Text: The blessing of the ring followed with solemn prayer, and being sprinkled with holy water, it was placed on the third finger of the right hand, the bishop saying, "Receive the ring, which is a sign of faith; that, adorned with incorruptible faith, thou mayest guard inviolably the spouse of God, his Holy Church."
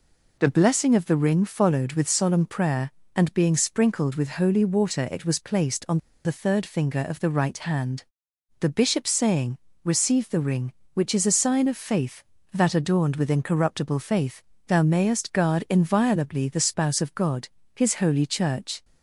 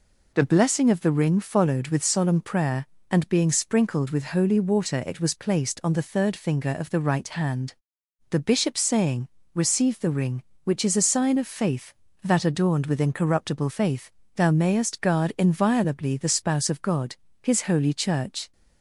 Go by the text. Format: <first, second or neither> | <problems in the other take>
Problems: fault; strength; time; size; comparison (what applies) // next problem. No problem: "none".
second | pauses between "on" and "the"; slight; at 5.9 s; 0.27 s long